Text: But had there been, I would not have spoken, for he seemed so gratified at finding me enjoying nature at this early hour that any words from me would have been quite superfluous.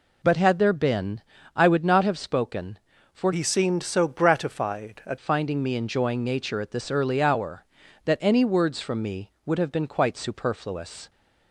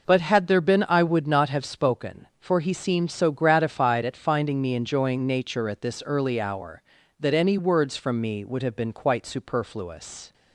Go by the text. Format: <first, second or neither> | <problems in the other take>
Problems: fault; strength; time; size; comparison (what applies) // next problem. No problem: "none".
second | changes voice from "he" to "at"; from 3.3 to 5.1 s; 1.8 s long